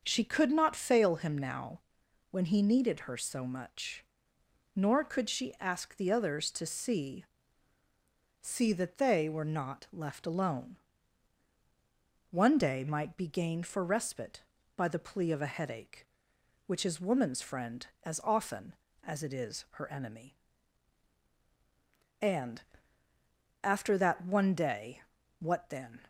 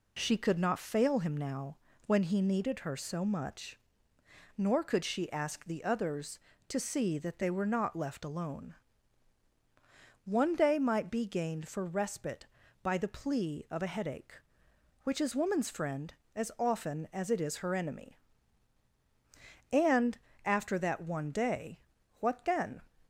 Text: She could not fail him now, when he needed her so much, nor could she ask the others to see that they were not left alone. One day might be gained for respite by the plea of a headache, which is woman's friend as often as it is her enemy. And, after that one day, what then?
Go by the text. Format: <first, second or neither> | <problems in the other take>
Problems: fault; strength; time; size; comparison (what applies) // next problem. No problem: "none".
second | says "see" twice; at 8.4 s